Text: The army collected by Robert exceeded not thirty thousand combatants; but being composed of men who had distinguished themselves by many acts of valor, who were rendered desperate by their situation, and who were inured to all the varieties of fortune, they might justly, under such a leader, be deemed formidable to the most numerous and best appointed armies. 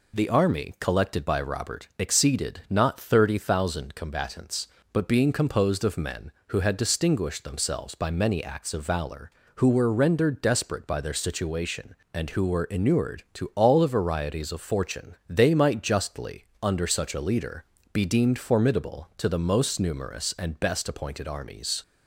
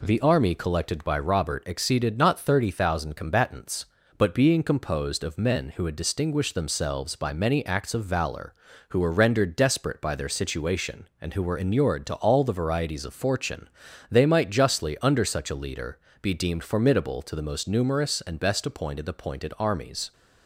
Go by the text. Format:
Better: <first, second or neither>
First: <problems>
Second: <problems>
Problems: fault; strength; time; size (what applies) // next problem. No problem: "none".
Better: first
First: none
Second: says "appointed" twice; at 19.0 s